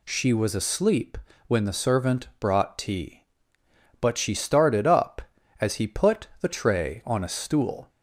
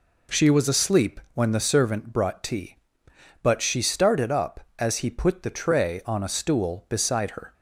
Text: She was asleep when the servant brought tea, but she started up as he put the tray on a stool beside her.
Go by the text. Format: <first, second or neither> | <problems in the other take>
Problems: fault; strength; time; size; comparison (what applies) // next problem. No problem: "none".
second | pauses between "asleep" and "when"; slight; at 1.1 s; 0.30 s long // stops before "beside her"; at 7.8 s